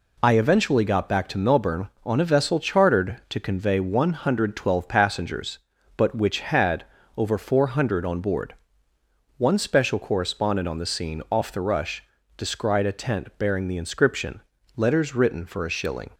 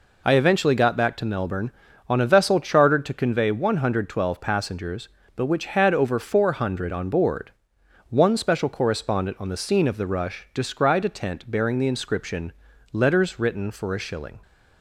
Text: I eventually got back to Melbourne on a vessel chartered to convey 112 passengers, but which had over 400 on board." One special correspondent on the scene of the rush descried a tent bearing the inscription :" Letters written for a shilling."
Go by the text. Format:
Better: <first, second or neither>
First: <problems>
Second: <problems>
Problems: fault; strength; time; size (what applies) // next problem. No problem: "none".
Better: second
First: pauses between "had" and "over"; slight; at 6.8 s; 0.30 s long // says "off" for "of"; at 11.3 s // pauses between "rush" and "descried"; slight; at 12.0 s; 0.32 s long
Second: none